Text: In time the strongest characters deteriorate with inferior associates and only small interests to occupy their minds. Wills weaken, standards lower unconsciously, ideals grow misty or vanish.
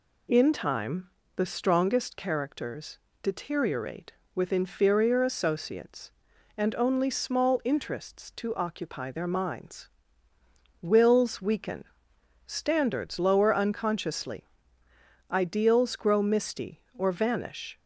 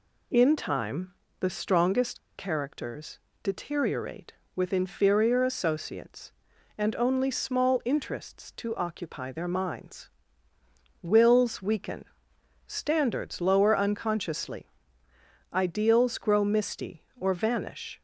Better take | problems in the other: first | pauses between "time" and "the"; slight; at 1.1 s; 0.28 s long; slight in the first // pauses between "strongest" and "characters"; slight; at 2.1 s; 0.18 s long // pauses between "characters" and "deteriorate"; slight; at 3.1 s; 0.24 s long; slight in the first

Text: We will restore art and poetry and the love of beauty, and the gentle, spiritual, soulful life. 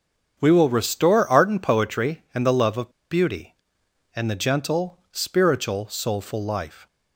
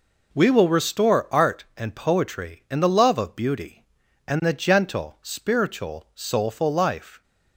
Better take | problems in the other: second | starts louder than the rest; strong; until 1.4 s; 7 dB // pauses between "of" and "beauty"; slight; at 2.9 s; 0.19 s long

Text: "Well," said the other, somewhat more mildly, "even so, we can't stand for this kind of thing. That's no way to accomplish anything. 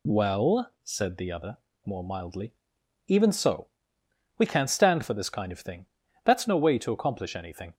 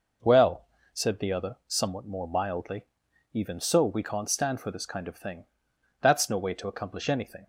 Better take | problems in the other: second | skips "somewhat"; at 1.7 s

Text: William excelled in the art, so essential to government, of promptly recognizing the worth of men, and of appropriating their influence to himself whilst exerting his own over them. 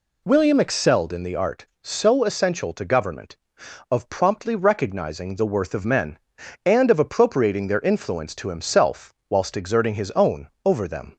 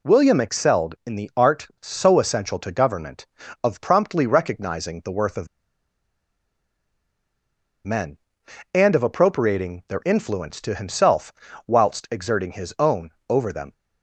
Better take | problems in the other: first | pauses between "of" and "men"; strong; at 5.4 s; 2.3 s long // pauses between "himself" and "whilst"; slight; at 11.3 s; 0.34 s long; slight in the first // pauses between "own" and "over"; slight; at 13.0 s; 0.22 s long; slight in the first

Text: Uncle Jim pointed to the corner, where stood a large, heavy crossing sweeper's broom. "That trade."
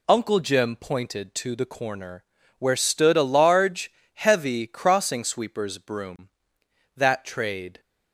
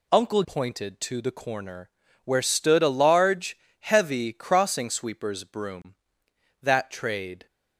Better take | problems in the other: first | skips "Jim"; at 0.4 s

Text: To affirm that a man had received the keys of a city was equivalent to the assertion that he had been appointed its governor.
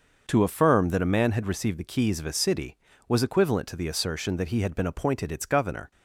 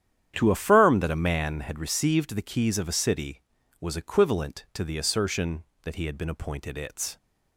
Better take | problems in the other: first | starts louder than the rest; strong; until 1.3 s; 9.5 dB; also in the first // stops before "governor"; at 7.1 s

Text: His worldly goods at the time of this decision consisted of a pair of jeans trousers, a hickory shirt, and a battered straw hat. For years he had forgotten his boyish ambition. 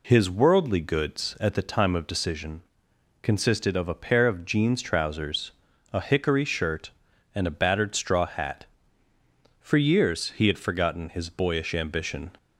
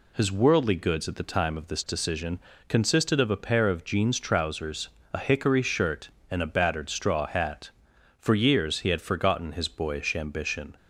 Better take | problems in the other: second | skips "this"; at 2.0 s // pauses between "decision" and "consisted"; noticeable; at 2.6 s; 0.61 s long; slight in the second

